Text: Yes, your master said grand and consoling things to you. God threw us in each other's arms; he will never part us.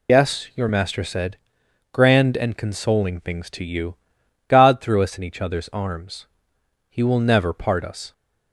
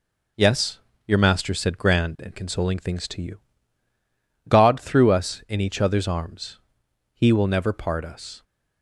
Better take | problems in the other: second | loses the start of "Yes"; at 0.0 s; 65 ms // pauses between "said" and "grand"; noticeable; at 1.3 s; 0.56 s long

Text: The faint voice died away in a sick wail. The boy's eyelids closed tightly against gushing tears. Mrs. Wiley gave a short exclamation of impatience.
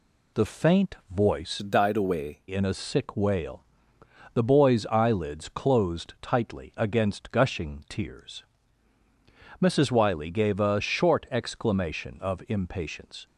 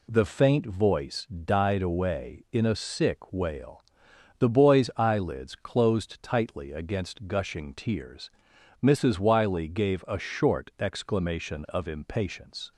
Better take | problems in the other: second | pauses between "faint" and "voice"; slight; at 0.9 s; 0.16 s long // changes voice from "died" to "away"; from 1.5 to 2.3 s; 0.8 s long

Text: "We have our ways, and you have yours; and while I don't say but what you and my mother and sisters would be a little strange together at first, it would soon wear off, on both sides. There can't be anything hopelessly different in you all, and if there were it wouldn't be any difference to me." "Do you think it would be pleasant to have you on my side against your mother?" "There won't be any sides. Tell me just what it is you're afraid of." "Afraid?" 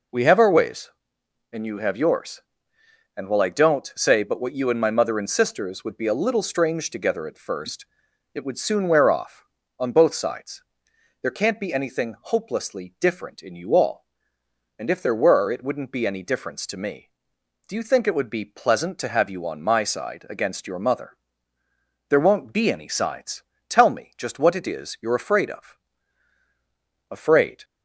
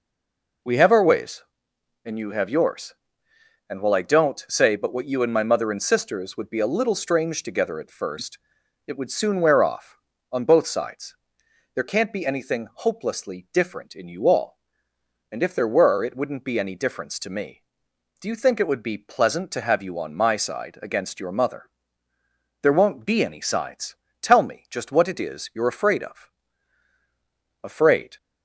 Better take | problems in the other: first | stays silent before the first word; slight; until 0.6 s; 0.6 s long

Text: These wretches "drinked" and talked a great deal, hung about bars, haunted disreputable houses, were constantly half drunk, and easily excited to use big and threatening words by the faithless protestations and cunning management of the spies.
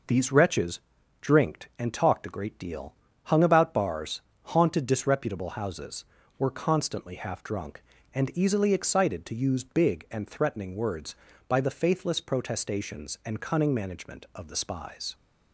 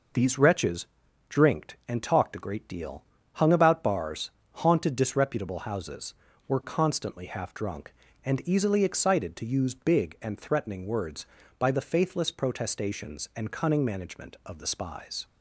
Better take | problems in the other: neither | pauses between "wretches" and "drinked"; the same in both

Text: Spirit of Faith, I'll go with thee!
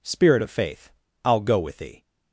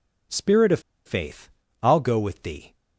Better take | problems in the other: first | pauses between "of" and "Faith"; slight; at 0.7 s; 0.26 s long

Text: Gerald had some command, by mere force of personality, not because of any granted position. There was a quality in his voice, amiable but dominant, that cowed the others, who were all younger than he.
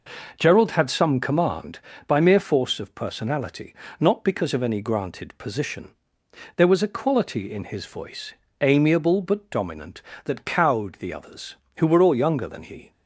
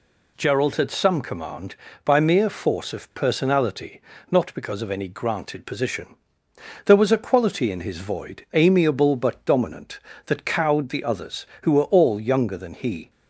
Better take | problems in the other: first | says "void" for "voice"; at 7.9 s

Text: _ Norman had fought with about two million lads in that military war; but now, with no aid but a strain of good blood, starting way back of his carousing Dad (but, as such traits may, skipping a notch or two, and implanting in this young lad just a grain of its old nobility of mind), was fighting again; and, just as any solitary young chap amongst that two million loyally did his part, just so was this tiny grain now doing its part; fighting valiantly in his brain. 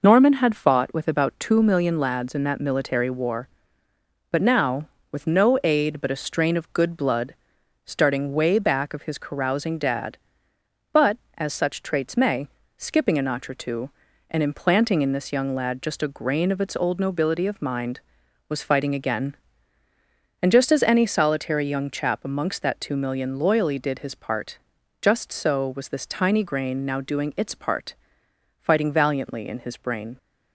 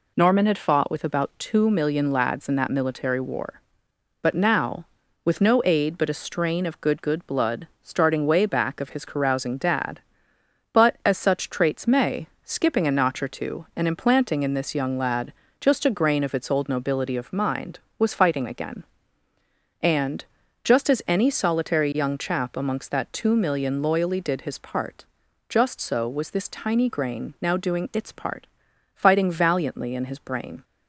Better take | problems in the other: first | says "good" twice; at 6.9 s // pauses between "lad" and "just"; slight; at 15.3 s; 0.28 s long

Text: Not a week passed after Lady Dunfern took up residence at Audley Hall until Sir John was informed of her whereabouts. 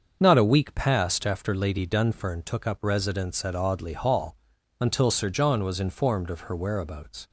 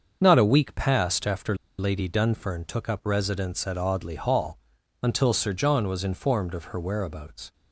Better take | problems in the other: first | starts louder than the rest; until 1.2 s; 7 dB; also in the first // pauses between "after" and "Lady"; slight; at 1.5 s; 0.21 s long // pauses between "Hall" and "until"; at 4.5 s; 0.42 s long; also in the first

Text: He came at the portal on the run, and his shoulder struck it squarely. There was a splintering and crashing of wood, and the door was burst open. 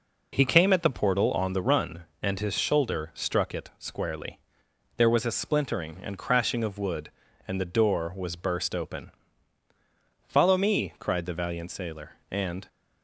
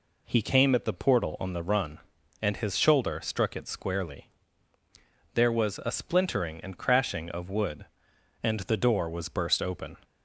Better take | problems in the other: second | goes on to say "Follow me cried the valiant sailor and"; strong; from 10.2 s on; 2.4 s long

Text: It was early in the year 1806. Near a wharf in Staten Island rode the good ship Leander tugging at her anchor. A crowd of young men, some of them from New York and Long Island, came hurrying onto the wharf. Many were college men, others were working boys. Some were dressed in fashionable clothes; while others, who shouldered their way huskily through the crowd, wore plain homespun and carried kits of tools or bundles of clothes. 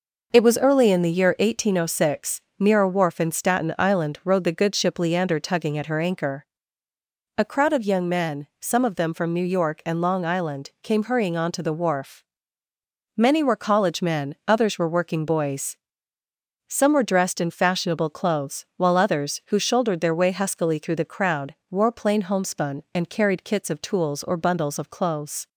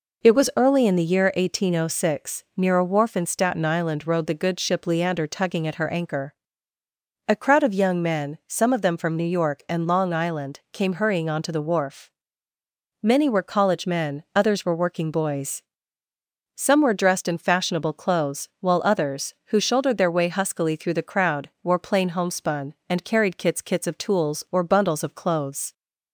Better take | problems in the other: first | says "kits" twice; at 23.6 s

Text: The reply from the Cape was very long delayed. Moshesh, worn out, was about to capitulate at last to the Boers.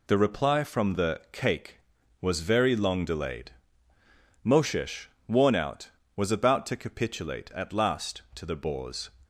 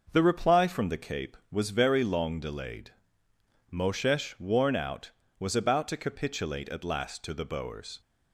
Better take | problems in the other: second | says "Cake" for "Cape"; at 1.3 s

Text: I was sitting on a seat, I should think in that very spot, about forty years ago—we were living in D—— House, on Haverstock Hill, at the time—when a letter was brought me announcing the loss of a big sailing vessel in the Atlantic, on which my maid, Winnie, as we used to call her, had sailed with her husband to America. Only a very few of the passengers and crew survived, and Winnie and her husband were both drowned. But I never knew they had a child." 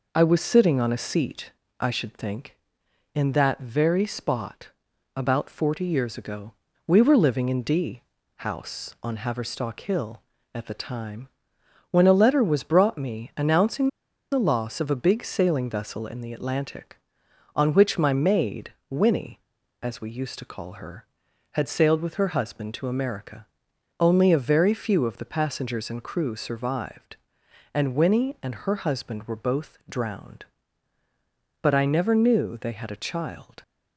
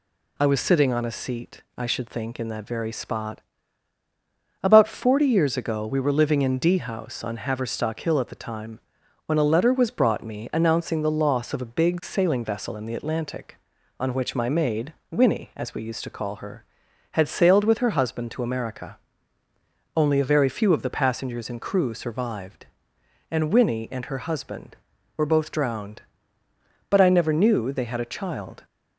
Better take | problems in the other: second | pauses between "announcing" and "the"; at 13.8 s; 0.43 s long

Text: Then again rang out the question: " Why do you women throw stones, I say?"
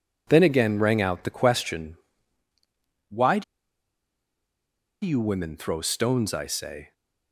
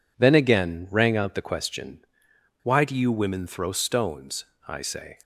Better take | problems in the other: second | pauses between "do" and "you"; strong; at 3.4 s; 1.6 s long

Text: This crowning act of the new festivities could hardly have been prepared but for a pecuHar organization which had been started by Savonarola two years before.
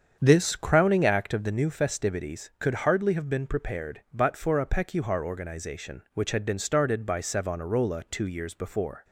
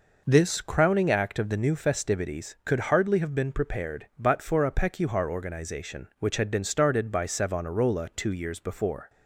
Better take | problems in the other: second | starts louder than the rest; strong; until 1.4 s; 7.5 dB

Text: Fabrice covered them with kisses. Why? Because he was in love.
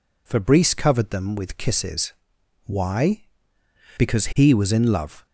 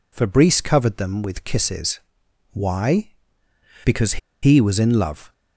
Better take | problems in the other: first | pauses between "Because" and "he"; slight; at 4.1 s; 0.24 s long

